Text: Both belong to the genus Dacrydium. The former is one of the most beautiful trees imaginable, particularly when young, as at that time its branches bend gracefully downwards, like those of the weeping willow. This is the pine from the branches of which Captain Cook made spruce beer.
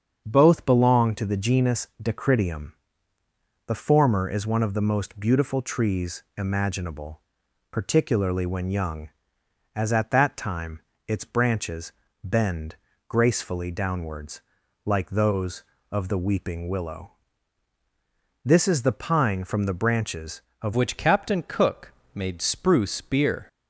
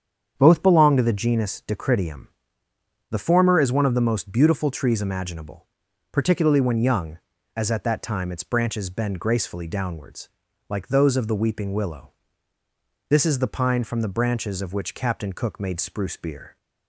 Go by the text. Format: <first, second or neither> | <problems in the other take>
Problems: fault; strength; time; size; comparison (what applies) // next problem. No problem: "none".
second | starts louder than the rest; strong; until 1.2 s; 7 dB; strong in the second // pauses between "time" and "its"; slight; at 10.7 s; 0.28 s long // pauses between "branches" and "bend"; slight; at 11.9 s; 0.30 s long // pauses between "bend" and "gracefully"; slight; at 12.7 s; 0.32 s long // changes voice at "which"; from 20.7 s on; 2.7 s long // pauses between "Cook" and "made"; slight; at 21.9 s; 0.22 s long